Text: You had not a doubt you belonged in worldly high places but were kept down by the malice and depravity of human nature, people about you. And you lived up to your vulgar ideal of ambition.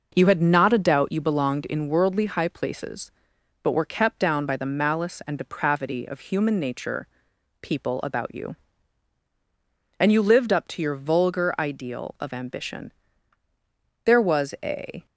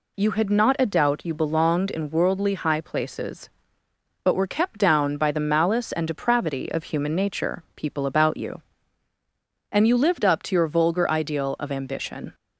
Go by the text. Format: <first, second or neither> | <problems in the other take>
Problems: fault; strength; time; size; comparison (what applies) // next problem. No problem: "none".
second | goes on to say "There was a"; noticeable; from 14.0 s on; 1.0 s long